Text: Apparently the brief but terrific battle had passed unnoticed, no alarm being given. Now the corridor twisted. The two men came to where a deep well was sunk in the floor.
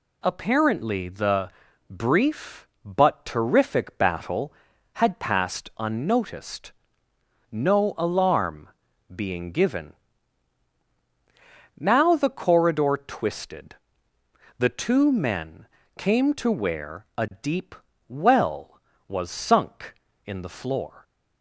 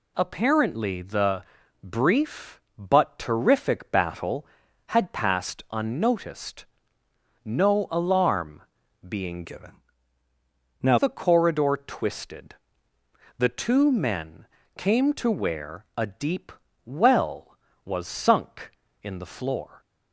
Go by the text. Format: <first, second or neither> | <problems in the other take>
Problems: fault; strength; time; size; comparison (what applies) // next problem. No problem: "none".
first | pauses between "the" and "brief"; at 1.4 s; 0.40 s long; also in the first // pauses between "alarm" and "being"; at 8.6 s; 0.44 s long; also in the first // changes voice from "given" to "Now"; from 9.4 to 10.9 s; 1.5 s long // pauses between "men" and "came"; slight; at 14.4 s; 0.32 s long; slight in the first // pauses between "deep" and "well"; slight; at 16.5 s; 0.34 s long; slight in the first